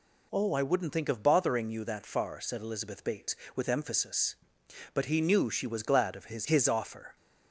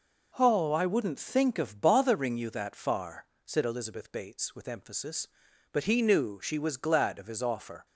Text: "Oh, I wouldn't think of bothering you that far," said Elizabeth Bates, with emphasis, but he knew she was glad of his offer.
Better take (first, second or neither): second